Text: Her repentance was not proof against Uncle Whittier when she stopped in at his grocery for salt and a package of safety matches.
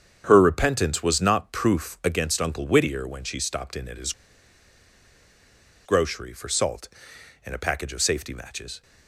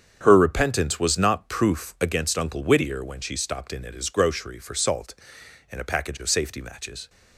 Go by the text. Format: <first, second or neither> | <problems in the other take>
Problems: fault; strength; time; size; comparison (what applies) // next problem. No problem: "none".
second | starts louder than the rest; strong; until 1.2 s; 7.5 dB; strong in the second // pauses between "his" and "grocery"; strong; at 4.1 s; 1.7 s long